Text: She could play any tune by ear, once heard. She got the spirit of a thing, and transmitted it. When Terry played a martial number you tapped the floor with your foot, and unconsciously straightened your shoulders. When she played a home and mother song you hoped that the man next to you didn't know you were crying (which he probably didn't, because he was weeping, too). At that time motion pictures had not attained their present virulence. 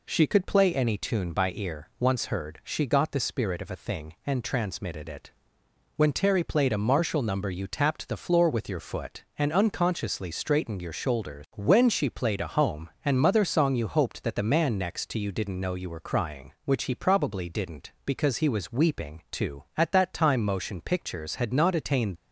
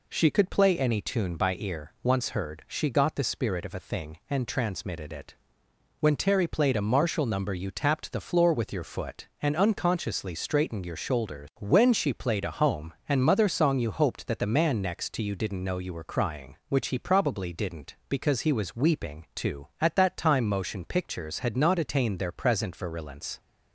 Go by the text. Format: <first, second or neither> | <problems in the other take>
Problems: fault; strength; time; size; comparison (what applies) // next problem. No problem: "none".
second | stops before "their present virulence"; at 22.1 s